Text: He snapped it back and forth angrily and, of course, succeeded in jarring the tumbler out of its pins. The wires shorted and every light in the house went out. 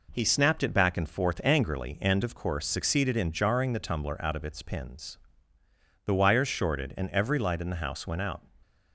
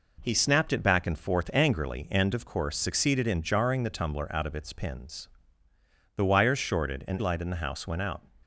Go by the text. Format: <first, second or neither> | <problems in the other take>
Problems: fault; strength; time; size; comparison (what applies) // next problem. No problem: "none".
first | skips "every"; at 7.1 s